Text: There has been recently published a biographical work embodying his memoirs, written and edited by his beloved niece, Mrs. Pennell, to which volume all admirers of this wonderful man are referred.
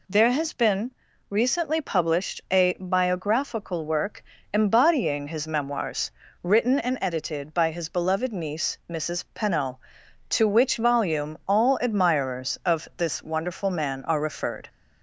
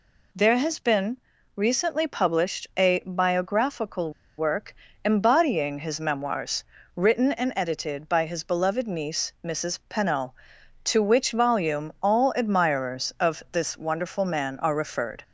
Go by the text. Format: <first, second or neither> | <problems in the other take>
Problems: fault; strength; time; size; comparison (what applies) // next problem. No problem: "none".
first | pauses between "been" and "recently"; at 1.1 s; 0.40 s long; also in the first // pauses between "biographical" and "work"; slight; at 4.1 s; 0.25 s long // pauses between "work" and "embodying"; slight; at 4.7 s; 0.30 s long; slight in the first